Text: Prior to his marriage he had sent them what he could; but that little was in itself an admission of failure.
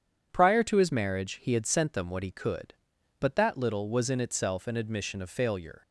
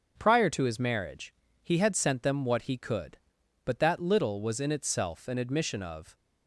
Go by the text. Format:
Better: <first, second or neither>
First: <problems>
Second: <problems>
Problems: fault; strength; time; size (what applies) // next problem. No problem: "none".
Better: first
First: starts louder than the rest; strong; until 1.3 s; 8 dB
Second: starts louder than the rest; until 1.1 s; 7 dB // pauses between "marriage" and "he"; slight; at 1.3 s; 0.28 s long // stops before "failure"; at 6.1 s